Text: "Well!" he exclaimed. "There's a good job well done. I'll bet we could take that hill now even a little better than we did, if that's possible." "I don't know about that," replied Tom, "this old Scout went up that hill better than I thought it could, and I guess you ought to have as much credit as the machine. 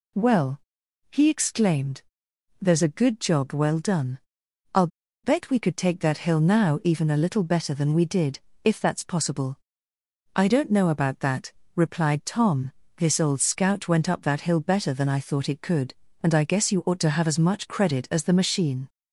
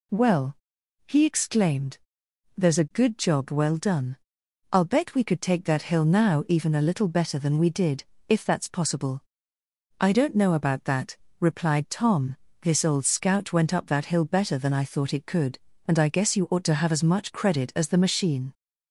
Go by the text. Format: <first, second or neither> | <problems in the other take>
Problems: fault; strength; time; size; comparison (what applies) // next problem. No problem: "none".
second | pauses between "I'll" and "bet"; at 4.8 s; 0.36 s long